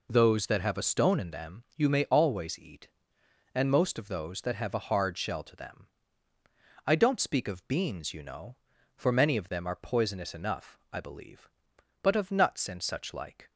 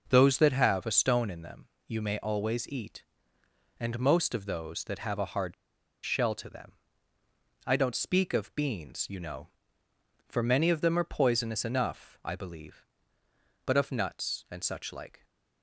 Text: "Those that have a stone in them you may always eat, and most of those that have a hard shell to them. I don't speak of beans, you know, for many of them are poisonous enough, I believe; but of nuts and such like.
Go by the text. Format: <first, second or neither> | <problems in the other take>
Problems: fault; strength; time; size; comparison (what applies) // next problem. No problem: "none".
first | pauses between "them" and "you"; slight; at 1.6 s; 0.22 s long // pauses between "hard" and "shell"; noticeable; at 5.5 s; 0.51 s long